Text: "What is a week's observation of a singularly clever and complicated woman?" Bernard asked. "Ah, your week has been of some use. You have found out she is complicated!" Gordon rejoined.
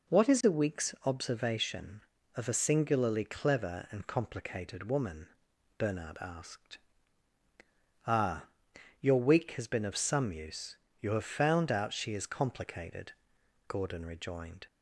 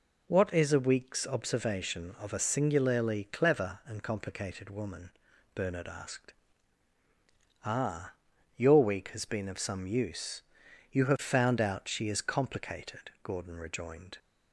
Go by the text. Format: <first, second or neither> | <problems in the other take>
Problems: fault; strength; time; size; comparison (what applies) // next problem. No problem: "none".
neither | none